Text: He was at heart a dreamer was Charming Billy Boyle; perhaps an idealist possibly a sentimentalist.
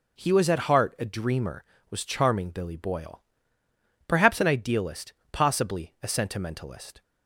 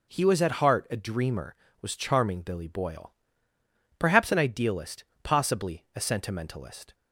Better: neither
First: pauses between "idealist" and "possibly"; slight; at 5.1 s; 0.18 s long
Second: pauses between "idealist" and "possibly"; slight; at 5.0 s; 0.18 s long

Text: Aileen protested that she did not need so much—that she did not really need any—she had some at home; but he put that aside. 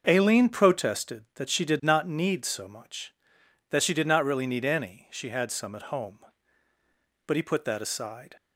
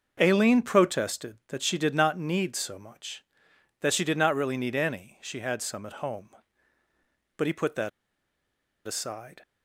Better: first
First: starts louder than the rest; noticeable; until 1.0 s; 6 dB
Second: starts louder than the rest; noticeable; until 1.2 s; 6 dB // pauses between "that" and "aside"; noticeable; at 7.8 s; 0.97 s long

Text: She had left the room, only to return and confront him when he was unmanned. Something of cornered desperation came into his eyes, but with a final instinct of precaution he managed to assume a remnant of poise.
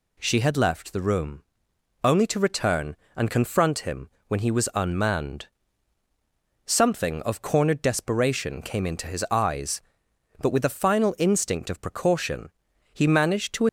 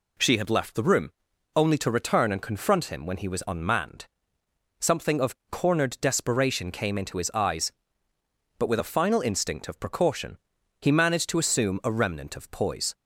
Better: second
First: pauses between "him" and "when"; slight; at 4.0 s; 0.18 s long // pauses between "precaution" and "he"; at 12.5 s; 0.42 s long // stops before "assume a remnant of poise"; at 13.6 s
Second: pauses between "precaution" and "he"; at 10.3 s; 0.42 s long

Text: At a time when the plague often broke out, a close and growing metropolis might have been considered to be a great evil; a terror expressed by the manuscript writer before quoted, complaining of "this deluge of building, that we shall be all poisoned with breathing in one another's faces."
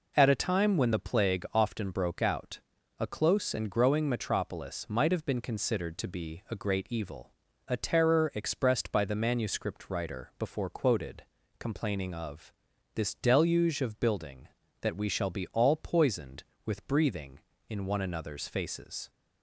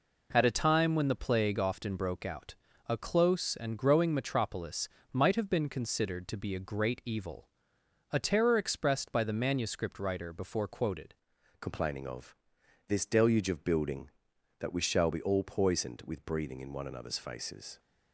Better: first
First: pauses between "of" and "this"; at 12.5 s; 0.44 s long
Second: pauses between "metropolis" and "might"; slight; at 4.8 s; 0.24 s long // changes voice at "complaining"; from 11.5 s on; 6.2 s long // pauses between "of" and "this"; noticeable; at 12.3 s; 0.54 s long

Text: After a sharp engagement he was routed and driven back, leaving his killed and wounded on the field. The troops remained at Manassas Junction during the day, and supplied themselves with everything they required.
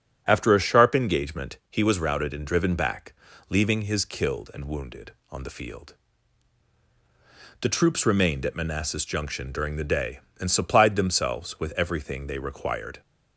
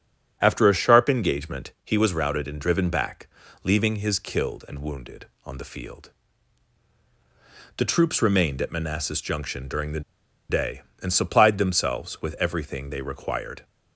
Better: first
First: starts louder than the rest; until 1.2 s; 7 dB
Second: starts louder than the rest; until 1.4 s; 7 dB // pauses between "the" and "day"; noticeable; at 10.0 s; 0.49 s long

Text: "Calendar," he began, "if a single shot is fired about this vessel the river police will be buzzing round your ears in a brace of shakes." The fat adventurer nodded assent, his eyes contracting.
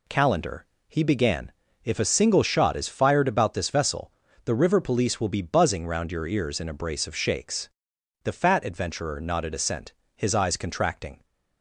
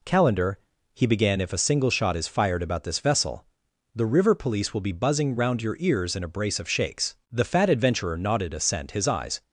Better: first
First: pauses between "vessel" and "the"; slight; at 4.1 s; 0.32 s long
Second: pauses between "vessel" and "the"; noticeable; at 3.4 s; 0.48 s long // stops before "contracting"; at 9.4 s

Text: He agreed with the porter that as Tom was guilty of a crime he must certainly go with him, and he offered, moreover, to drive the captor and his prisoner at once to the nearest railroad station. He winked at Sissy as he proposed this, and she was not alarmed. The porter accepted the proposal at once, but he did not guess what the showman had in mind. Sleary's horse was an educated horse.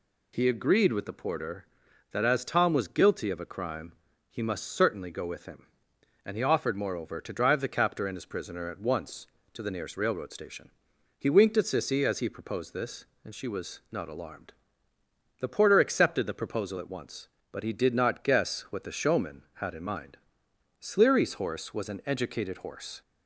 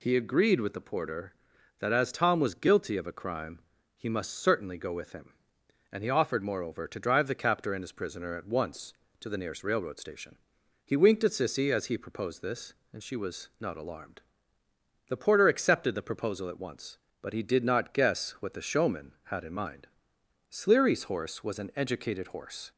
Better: neither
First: pauses between "crime" and "he"; slight; at 3.9 s; 0.36 s long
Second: pauses between "crime" and "he"; slight; at 3.5 s; 0.36 s long

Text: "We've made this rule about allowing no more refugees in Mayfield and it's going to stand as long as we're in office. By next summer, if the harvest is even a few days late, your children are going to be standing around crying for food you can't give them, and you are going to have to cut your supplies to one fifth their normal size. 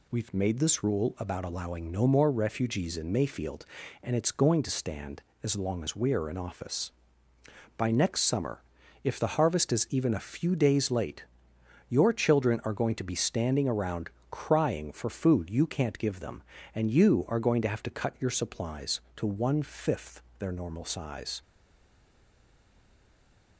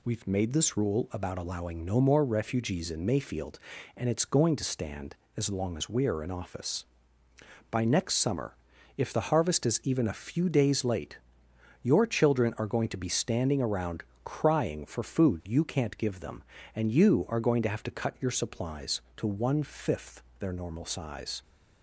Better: second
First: pauses between "around" and "crying"; slight; at 14.0 s; 0.22 s long // pauses between "fifth" and "their"; slight; at 20.2 s; 0.18 s long // stays silent after the last word; from 21.4 s on; 2.1 s long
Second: pauses between "around" and "crying"; slight; at 14.0 s; 0.22 s long // pauses between "fifth" and "their"; slight; at 20.2 s; 0.18 s long

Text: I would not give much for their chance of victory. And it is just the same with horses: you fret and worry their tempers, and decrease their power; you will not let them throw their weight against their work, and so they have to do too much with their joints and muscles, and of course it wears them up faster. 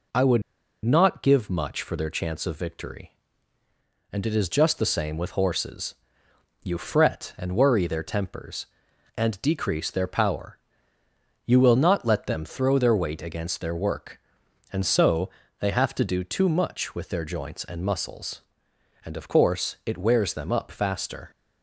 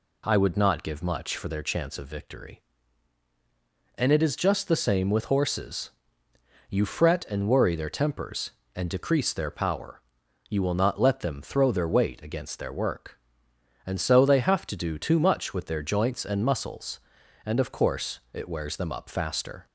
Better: second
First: pauses between "would" and "not"; at 0.4 s; 0.43 s long // pauses between "so" and "they"; slight; at 15.2 s; 0.30 s long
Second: none

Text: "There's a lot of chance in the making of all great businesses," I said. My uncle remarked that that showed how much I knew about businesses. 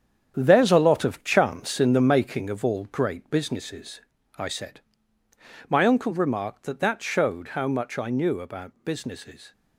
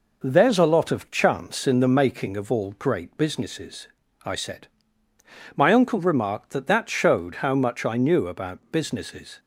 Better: second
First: gets quieter; strong; throughout; 9 dB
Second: none

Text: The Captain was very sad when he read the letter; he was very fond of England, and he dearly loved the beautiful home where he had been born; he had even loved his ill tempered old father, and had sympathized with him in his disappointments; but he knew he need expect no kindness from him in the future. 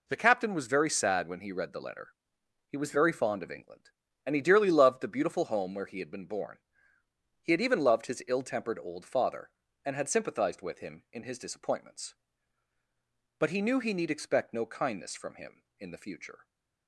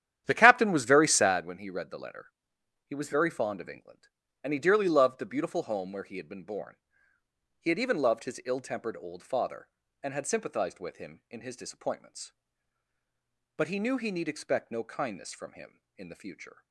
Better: first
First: none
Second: starts louder than the rest; strong; until 1.4 s; 10.5 dB

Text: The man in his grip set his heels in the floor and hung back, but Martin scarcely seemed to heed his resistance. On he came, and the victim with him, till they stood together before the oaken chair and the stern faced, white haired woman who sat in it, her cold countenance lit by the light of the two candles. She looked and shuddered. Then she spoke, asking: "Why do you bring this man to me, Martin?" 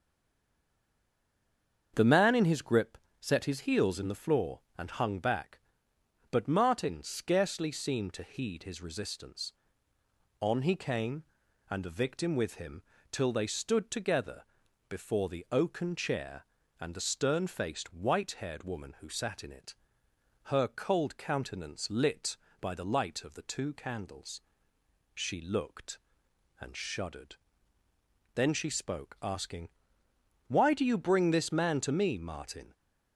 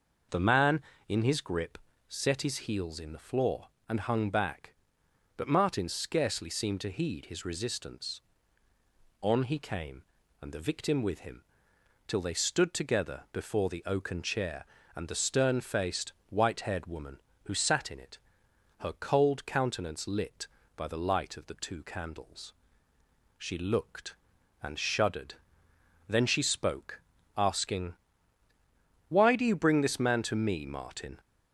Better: second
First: stays silent before the first word; noticeable; until 1.9 s; 1.9 s long // starts louder than the rest; strong; until 2.9 s; 7 dB // pauses between "grip" and "set"; slight; at 2.9 s; 0.24 s long // pauses between "together" and "before"; noticeable; at 14.4 s; 0.46 s long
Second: pauses between "grip" and "set"; slight; at 1.7 s; 0.28 s long

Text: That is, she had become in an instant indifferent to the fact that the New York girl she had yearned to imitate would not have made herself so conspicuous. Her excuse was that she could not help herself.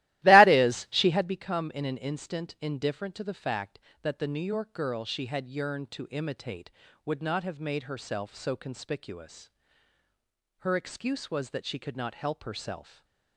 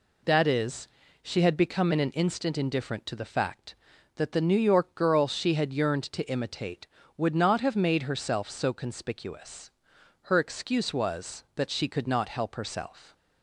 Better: second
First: starts louder than the rest; strong; until 1.4 s; 16 dB // stays silent after the last word; slight; from 12.8 s on; 0.5 s long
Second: none

